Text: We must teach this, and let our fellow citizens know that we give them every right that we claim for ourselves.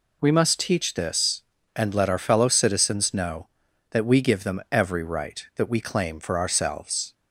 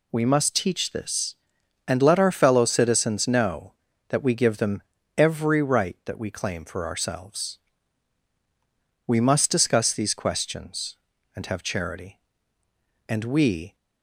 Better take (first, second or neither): first